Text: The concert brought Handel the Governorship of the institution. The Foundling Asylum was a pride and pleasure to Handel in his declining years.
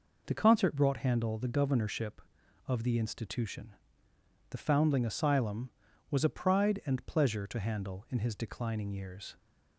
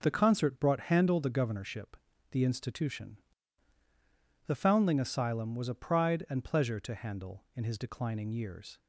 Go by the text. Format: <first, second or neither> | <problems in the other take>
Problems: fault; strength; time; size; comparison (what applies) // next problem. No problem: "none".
first | skips "of"; at 2.1 s